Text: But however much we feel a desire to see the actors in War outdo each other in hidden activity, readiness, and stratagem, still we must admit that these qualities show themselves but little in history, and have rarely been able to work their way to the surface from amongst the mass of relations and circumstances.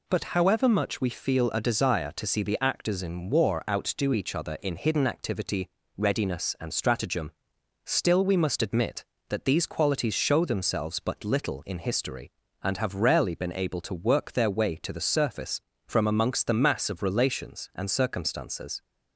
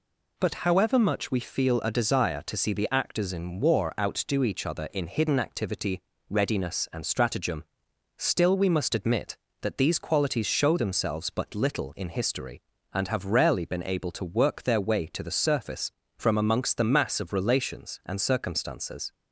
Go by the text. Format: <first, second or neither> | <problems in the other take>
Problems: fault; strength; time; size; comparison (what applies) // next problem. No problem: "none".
neither | none